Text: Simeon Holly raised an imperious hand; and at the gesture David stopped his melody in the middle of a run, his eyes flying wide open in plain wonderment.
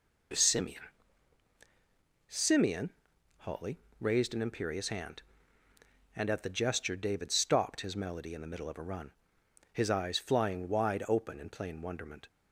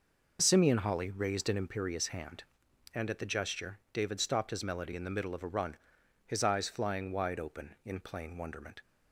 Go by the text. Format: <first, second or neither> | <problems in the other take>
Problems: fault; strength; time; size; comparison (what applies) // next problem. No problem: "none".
second | says "Simeon" twice; at 2.3 s // pauses between "Holly" and "raised"; slight; at 3.7 s; 0.24 s long